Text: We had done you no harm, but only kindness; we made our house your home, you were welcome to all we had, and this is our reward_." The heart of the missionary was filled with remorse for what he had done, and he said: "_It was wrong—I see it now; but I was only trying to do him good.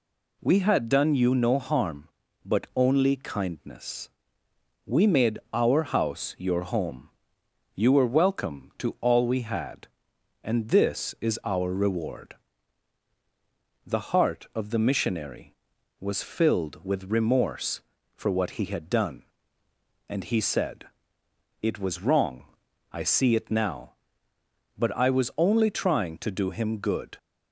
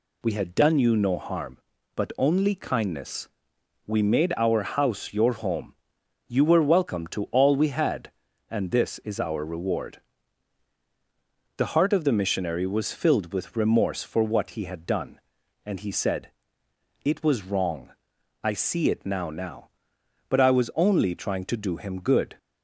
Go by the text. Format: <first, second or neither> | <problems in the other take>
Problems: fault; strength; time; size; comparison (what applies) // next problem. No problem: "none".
first | says "now" twice; at 19.2 s